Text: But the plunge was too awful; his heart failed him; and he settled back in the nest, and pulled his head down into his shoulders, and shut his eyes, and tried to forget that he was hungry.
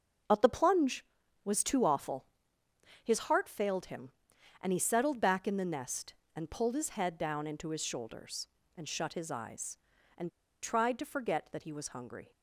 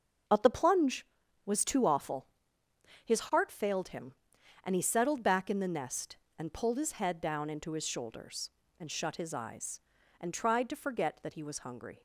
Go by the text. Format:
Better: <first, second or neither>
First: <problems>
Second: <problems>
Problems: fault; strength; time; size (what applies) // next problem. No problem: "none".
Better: second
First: starts louder than the rest; until 1.6 s; 7 dB // pauses between "and" and "tried"; slight; at 10.3 s; 0.32 s long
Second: starts louder than the rest; until 1.6 s; 7 dB